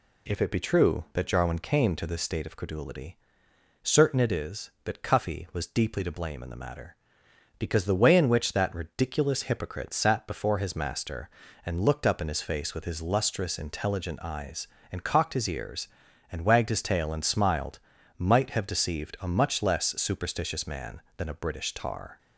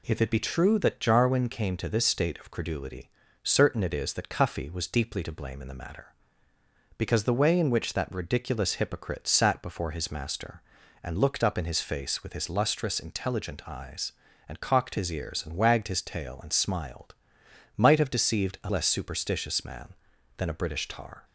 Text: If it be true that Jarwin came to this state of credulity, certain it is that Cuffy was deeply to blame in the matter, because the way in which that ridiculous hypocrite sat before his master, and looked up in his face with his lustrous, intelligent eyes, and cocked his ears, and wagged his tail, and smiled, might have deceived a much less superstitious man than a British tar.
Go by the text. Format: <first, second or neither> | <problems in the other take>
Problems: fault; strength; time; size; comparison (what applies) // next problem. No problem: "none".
first | skips "much"; at 18.6 s